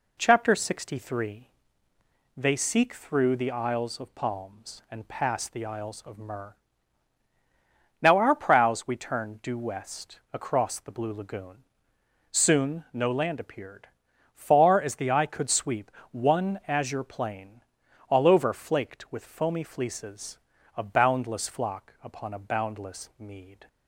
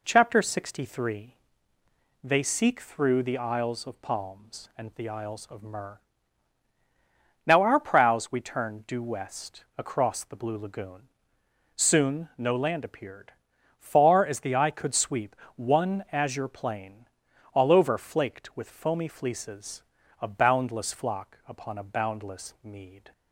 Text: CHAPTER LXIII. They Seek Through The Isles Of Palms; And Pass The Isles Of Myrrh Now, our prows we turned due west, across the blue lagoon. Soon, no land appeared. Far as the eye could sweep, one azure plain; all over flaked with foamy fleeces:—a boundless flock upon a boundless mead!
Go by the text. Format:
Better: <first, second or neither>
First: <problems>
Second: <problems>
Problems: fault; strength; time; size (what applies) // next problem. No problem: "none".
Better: first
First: pauses between "Myrrh" and "Now"; strong; at 6.5 s; 1.4 s long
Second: skips "Pass"; at 4.9 s // pauses between "Myrrh" and "Now"; strong; at 5.9 s; 1.4 s long